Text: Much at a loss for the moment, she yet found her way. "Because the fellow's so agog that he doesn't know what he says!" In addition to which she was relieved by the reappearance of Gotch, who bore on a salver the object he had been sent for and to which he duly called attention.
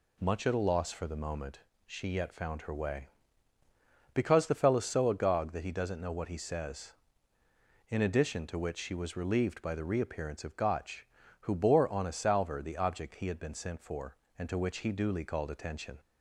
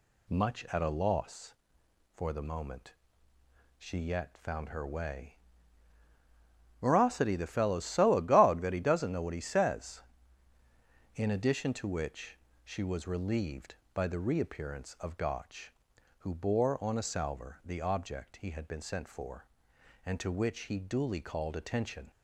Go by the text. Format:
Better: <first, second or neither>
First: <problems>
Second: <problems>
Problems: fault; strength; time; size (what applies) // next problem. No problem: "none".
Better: first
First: none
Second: says "Morosity" for "Because"; at 6.8 s // pauses between "which" and "she"; slight; at 12.3 s; 0.26 s long